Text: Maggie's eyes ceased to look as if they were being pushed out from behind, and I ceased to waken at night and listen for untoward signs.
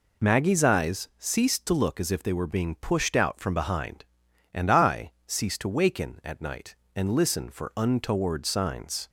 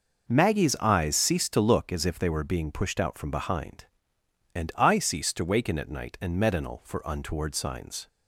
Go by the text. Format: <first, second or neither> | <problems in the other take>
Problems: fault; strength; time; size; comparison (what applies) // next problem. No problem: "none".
first | says "medinal" for "listen"; at 6.3 s